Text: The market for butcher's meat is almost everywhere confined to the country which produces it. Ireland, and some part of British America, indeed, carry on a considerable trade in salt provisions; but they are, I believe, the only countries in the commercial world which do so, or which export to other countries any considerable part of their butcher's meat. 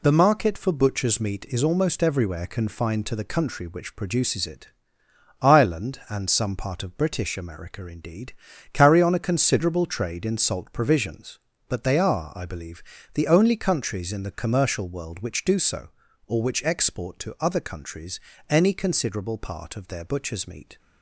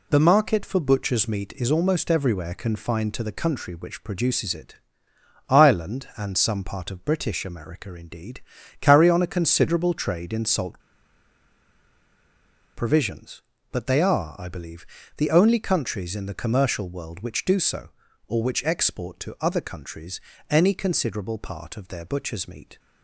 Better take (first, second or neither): first